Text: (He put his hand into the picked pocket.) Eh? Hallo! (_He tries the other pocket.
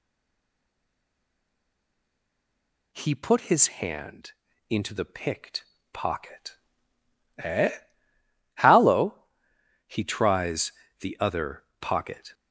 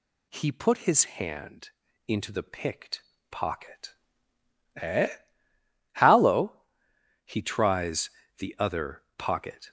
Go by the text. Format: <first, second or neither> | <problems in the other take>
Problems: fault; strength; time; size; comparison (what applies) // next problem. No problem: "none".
second | stays silent before the first word; strong; until 2.9 s; 2.9 s long // pauses between "hand" and "into"; slight; at 4.3 s; 0.36 s long; slight in the second // pauses between "picked" and "pocket"; slight; at 5.6 s; 0.30 s long; slight in the second // pauses between "tries" and "the"; slight; at 10.7 s; 0.26 s long; slight in the second // pauses between "other" and "pocket"; slight; at 11.6 s; 0.18 s long; slight in the second